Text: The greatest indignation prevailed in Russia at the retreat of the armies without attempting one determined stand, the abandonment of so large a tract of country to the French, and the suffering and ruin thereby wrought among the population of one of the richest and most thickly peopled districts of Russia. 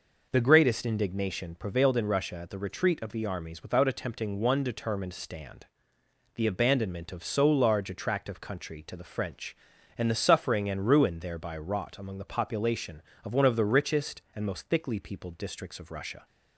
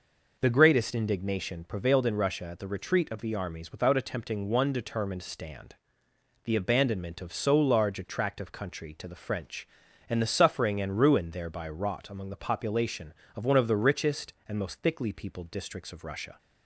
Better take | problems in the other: neither | none

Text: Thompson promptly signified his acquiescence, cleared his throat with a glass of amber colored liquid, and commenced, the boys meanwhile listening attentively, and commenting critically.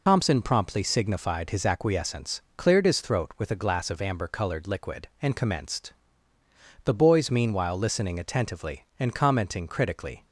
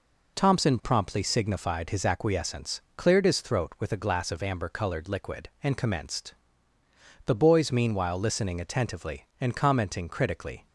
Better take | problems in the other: second | loses the start of "Thompson"; at 0.0 s; 70 ms

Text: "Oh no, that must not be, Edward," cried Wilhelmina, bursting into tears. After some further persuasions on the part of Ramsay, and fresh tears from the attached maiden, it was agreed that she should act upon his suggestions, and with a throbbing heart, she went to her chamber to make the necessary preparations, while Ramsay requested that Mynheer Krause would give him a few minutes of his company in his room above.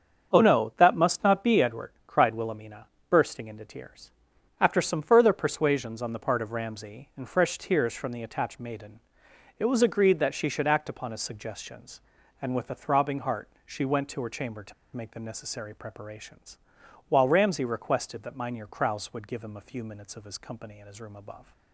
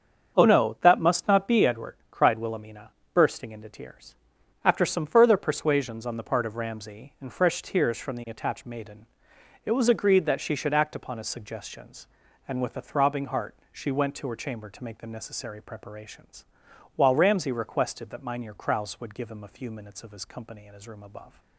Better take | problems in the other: second | starts louder than the rest; until 1.3 s; 7 dB; also in the second // pauses between "to" and "make"; slight; at 14.7 s; 0.22 s long

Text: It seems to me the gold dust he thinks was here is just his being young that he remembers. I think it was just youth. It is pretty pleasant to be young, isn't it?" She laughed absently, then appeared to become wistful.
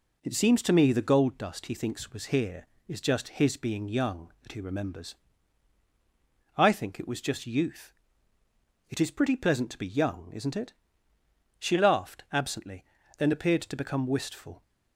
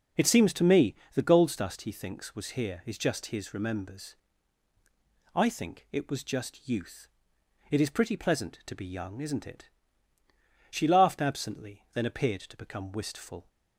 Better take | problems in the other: first | starts louder than the rest; noticeable; until 1.4 s; 6 dB // pauses between "me" and "the"; slight; at 0.9 s; 0.20 s long // skips "being young that he"; at 3.5 s

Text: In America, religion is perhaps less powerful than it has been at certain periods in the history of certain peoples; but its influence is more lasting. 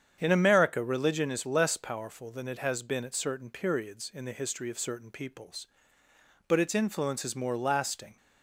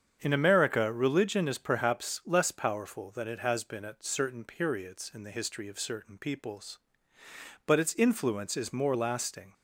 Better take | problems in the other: second | starts louder than the rest; strong; until 1.2 s; 8 dB; strong in the second // skips "perhaps"; at 1.4 s

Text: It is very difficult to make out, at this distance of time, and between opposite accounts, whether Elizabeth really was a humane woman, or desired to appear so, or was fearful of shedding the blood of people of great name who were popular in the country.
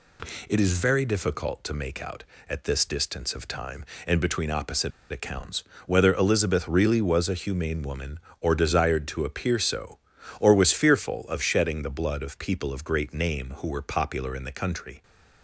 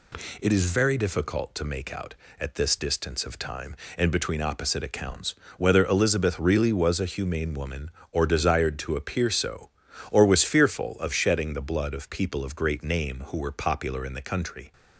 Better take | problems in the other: second | pauses between "opposite" and "accounts"; slight; at 4.9 s; 0.21 s long

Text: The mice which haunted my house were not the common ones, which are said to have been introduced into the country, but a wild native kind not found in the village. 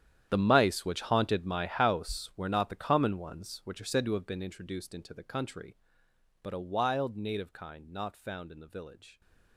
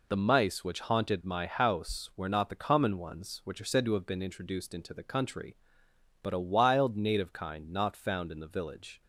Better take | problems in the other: second | gets quieter; strong; throughout; 17.5 dB

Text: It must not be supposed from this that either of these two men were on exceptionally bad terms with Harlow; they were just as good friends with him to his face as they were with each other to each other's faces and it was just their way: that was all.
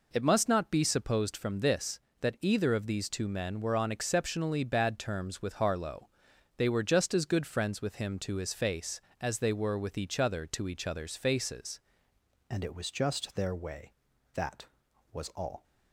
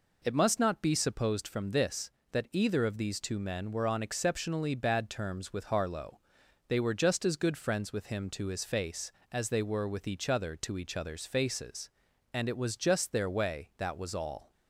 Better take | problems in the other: second | changes voice at "and"; from 12.4 s on; 3.2 s long

